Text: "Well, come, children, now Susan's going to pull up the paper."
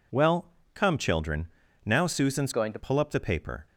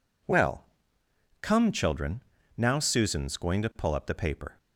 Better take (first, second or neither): second